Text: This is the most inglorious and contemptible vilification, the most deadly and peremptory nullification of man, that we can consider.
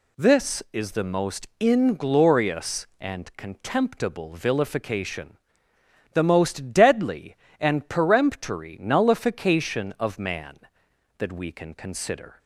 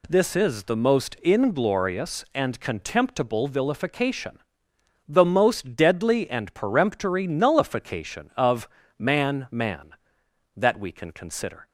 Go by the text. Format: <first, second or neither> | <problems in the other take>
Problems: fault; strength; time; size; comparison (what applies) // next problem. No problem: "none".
first | pauses between "of" and "man"; slight; at 8.6 s; 0.30 s long // says "man" twice; at 9.5 s